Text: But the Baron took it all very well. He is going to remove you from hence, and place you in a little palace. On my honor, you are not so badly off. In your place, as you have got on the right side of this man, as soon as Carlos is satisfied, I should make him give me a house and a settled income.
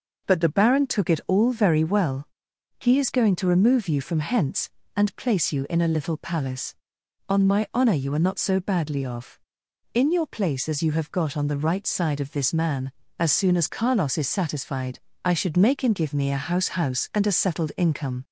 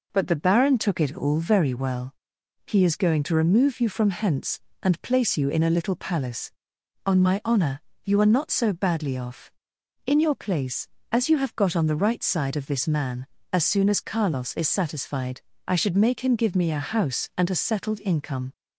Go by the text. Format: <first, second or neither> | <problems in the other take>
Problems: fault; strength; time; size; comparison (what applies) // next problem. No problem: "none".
second | says "house" twice; at 16.6 s